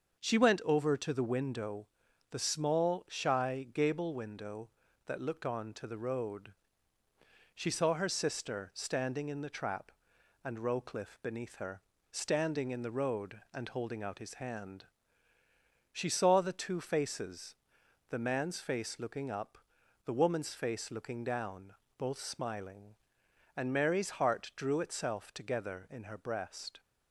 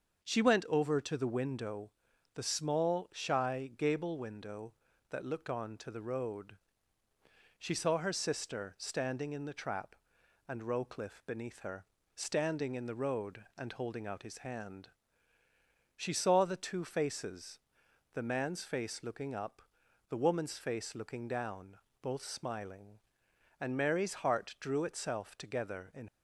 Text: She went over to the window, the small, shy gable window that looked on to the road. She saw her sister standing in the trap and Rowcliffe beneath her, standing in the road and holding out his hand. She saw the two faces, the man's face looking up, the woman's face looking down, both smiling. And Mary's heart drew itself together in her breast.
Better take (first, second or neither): first